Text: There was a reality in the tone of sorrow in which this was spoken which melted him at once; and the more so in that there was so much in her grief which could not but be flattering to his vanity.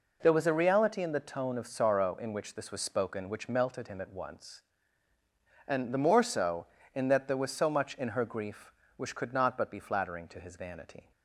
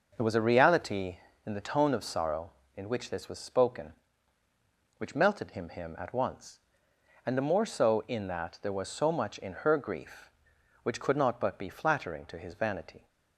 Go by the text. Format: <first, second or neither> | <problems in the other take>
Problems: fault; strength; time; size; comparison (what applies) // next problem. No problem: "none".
first | starts louder than the rest; noticeable; until 1.1 s; 6 dB // says "him" twice; at 5.6 s